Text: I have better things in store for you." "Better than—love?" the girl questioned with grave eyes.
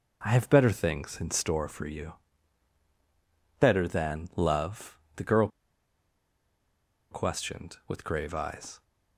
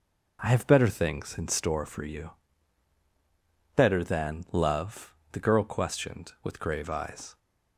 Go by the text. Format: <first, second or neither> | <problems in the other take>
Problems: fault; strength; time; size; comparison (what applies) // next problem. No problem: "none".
second | pauses between "girl" and "questioned"; strong; at 5.4 s; 1.6 s long